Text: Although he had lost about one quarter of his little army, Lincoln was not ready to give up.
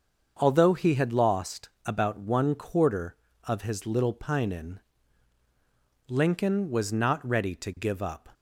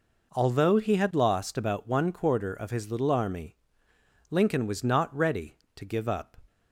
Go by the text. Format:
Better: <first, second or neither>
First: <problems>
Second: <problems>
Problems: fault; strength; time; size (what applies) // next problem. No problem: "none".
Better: second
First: starts louder than the rest; until 1.4 s; 6.5 dB // pauses between "lost" and "about"; slight; at 1.6 s; 0.16 s long // says "pinin" for "army"; at 4.1 s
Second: none